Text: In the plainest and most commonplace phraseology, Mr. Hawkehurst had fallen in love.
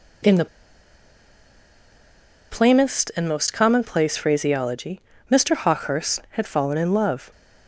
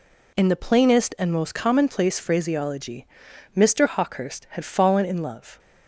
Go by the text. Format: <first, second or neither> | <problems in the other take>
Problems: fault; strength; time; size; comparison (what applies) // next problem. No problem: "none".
second | pauses between "the" and "plainest"; strong; at 0.4 s; 2.0 s long